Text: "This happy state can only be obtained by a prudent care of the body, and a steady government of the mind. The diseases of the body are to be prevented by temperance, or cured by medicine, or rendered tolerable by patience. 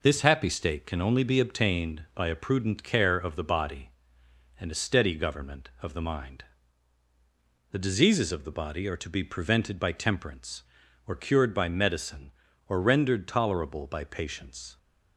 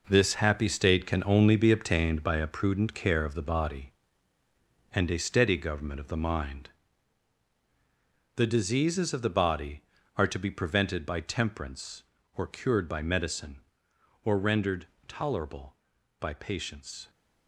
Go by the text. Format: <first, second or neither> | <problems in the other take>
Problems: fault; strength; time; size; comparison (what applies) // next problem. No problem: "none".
first | gets quieter; strong; throughout; 9.5 dB // pauses between "rendered" and "tolerable"; slight; at 14.8 s; 0.20 s long